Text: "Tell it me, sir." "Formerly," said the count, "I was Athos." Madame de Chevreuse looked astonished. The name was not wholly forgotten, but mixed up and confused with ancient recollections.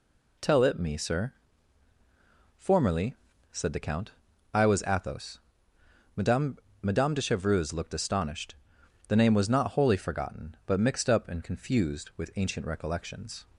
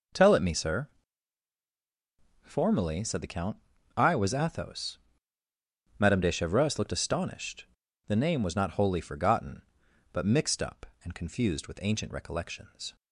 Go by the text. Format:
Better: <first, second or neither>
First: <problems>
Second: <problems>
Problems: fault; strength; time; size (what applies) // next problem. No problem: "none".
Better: second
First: says "Madame" twice; at 6.7 s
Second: none